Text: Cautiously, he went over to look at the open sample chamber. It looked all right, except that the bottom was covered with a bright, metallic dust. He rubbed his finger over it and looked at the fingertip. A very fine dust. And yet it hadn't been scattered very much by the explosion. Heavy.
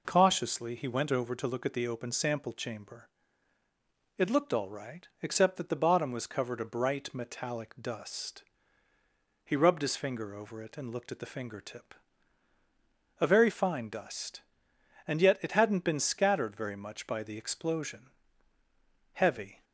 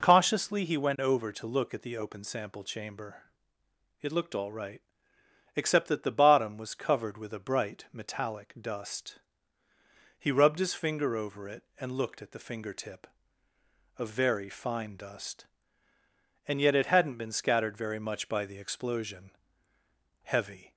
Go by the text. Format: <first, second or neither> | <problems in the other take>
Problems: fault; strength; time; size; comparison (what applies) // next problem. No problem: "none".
second | skips "with"; at 6.5 s